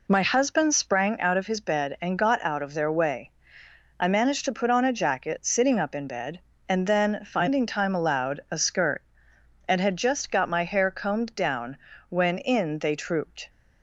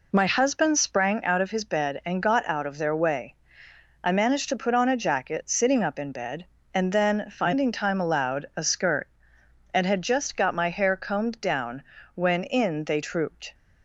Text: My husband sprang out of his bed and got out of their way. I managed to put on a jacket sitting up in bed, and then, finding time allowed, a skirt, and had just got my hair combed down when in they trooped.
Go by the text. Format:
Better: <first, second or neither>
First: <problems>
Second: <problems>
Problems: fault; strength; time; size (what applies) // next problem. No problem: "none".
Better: neither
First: pauses between "down" and "when"; slight; at 11.7 s; 0.32 s long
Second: pauses between "down" and "when"; slight; at 11.8 s; 0.32 s long